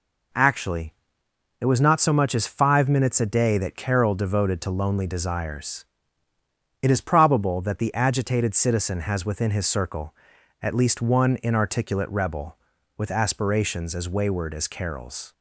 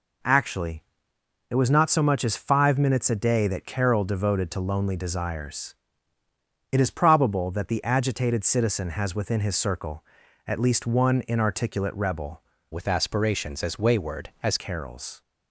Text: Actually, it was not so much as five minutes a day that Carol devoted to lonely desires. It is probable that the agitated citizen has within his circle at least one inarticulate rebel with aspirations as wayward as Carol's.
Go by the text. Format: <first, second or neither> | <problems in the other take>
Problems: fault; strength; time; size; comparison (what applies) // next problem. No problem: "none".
first | changes voice from "with" to "as"; from 12.7 to 14.5 s; 1.8 s long